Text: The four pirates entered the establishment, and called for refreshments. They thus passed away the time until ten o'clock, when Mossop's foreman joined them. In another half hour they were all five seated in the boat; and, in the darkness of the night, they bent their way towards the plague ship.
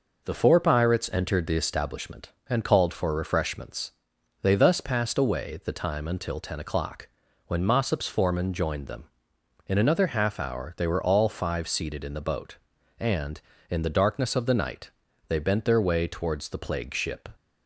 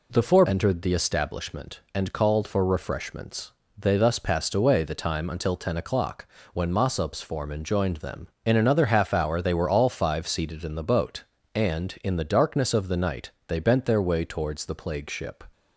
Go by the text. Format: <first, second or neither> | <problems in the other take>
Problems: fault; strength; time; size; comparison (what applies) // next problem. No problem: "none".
first | skips "pirates"; at 0.4 s